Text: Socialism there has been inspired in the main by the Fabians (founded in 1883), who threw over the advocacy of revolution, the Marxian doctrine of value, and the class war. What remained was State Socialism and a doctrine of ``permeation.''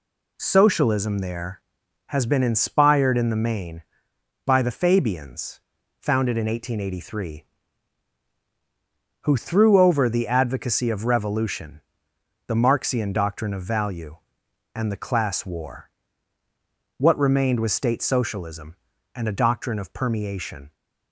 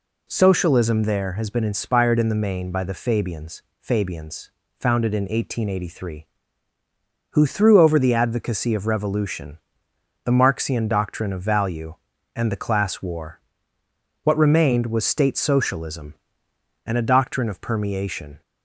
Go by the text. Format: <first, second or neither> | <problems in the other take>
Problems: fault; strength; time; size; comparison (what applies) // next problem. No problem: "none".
first | says "Fabians" twice; at 3.7 s